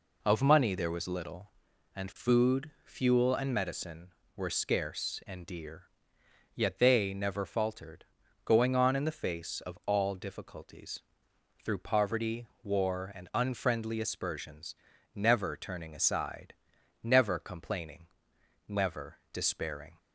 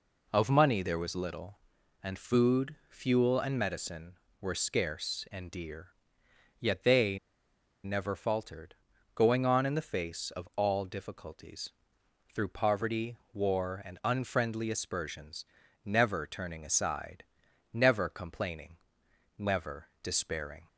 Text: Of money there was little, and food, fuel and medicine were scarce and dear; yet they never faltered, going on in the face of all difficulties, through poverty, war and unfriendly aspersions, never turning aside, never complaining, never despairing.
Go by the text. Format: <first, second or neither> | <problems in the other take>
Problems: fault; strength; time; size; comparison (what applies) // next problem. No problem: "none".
first | pauses between "they" and "never"; noticeable; at 7.1 s; 0.65 s long // pauses between "never" and "despairing"; slight; at 19.8 s; 0.16 s long; slight in the first